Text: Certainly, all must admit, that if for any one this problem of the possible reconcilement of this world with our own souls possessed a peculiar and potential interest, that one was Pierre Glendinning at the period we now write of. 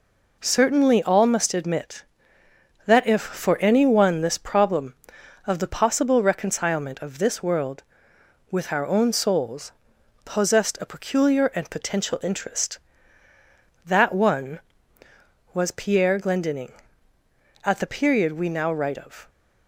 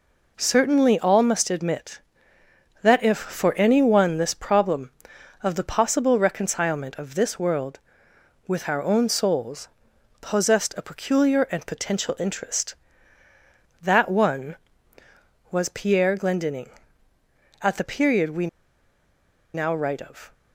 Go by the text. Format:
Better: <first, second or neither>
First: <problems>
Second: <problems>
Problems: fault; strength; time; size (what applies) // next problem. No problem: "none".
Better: first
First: pauses between "souls" and "possessed"; noticeable; at 9.7 s; 0.52 s long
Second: pauses between "souls" and "possessed"; noticeable; at 9.6 s; 0.52 s long // pauses between "we" and "now"; at 18.4 s; 1.0 s long